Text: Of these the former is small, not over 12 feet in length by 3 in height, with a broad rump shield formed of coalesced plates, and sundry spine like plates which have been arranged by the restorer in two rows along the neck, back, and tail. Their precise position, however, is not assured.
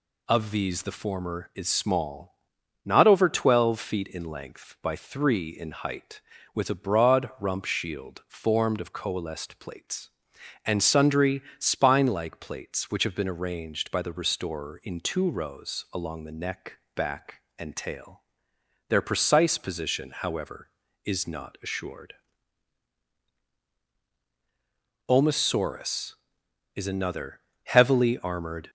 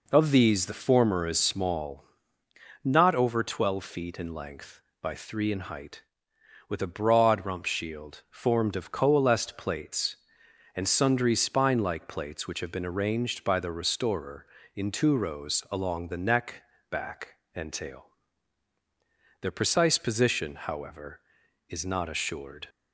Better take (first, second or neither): second